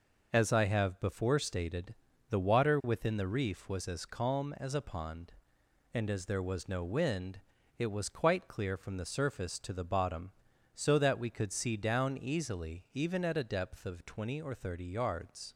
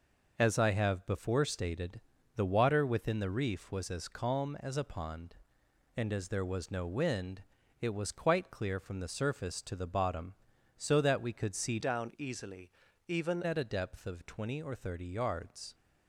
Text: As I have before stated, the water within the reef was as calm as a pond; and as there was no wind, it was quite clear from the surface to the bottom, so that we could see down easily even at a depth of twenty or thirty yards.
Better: first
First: none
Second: changes voice from "down" to "even"; from 11.8 to 13.4 s; 1.6 s long // pauses between "easily" and "even"; slight; at 12.7 s; 0.36 s long

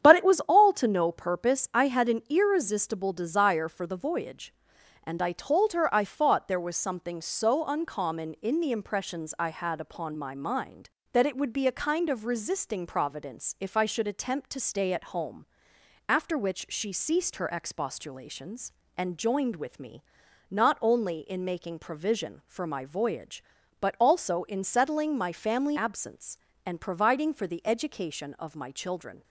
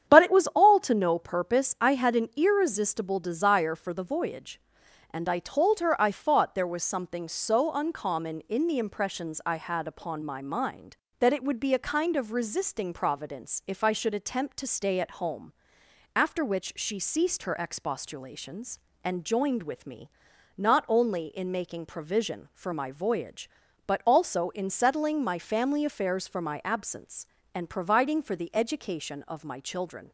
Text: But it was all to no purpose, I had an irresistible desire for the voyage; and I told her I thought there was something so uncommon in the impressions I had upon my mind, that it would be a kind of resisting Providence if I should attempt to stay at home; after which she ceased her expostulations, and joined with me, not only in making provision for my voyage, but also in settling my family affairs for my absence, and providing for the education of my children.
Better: second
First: starts louder than the rest; strong; until 1.0 s; 9 dB // skips "affairs for my"; at 25.7 s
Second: starts louder than the rest; strong; until 1.1 s; 9 dB

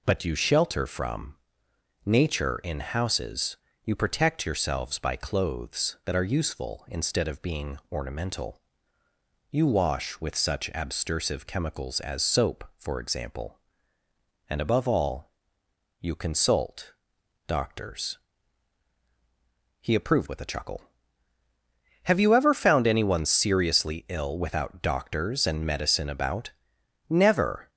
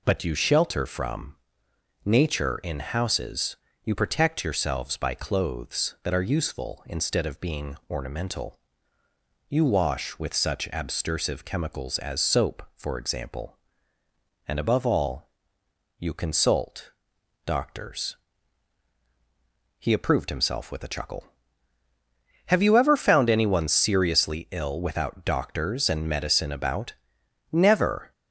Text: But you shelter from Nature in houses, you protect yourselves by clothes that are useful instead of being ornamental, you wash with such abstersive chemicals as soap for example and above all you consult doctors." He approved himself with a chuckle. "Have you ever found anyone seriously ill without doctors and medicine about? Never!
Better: second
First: pauses between "from" and "Nature"; noticeable; at 1.3 s; 0.70 s long // pauses between "all" and "you"; noticeable; at 15.2 s; 0.72 s long // pauses between "consult" and "doctors"; noticeable; at 16.9 s; 0.54 s long // skips "himself"; at 20.2 s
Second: pauses between "from" and "Nature"; noticeable; at 1.3 s; 0.70 s long // pauses between "all" and "you"; noticeable; at 15.2 s; 0.72 s long // pauses between "consult" and "doctors"; noticeable; at 16.8 s; 0.54 s long

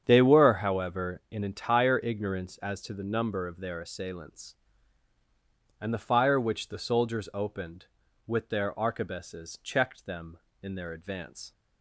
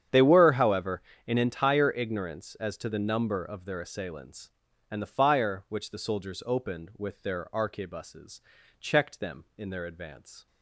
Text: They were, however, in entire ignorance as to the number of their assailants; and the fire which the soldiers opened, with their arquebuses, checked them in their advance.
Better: neither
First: starts louder than the rest; strong; until 1.0 s; 8 dB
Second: starts louder than the rest; strong; until 1.3 s; 9 dB

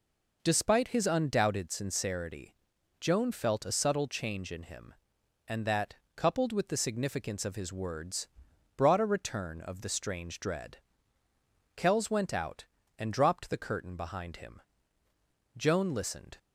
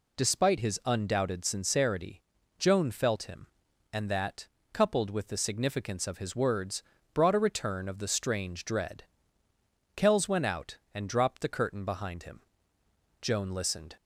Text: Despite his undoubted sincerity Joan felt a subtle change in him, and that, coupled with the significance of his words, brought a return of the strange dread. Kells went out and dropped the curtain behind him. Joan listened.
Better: first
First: pauses between "sincerity" and "Joan"; at 2.5 s; 0.44 s long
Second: pauses between "sincerity" and "Joan"; at 2.2 s; 0.38 s long // skips "a subtle change in"; at 3.2 s

